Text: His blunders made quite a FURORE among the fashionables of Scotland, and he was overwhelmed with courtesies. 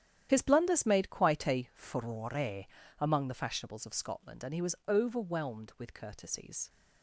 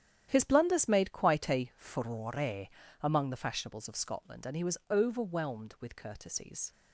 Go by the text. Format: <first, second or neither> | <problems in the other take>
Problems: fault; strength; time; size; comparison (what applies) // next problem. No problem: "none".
second | loses the start of "His"; at 0.2 s; 35 ms // starts louder than the rest; strong; until 1.3 s; 10.5 dB; strong in the second // pauses between "FURORE" and "among"; slight; at 2.6 s; 0.34 s long; slight in the second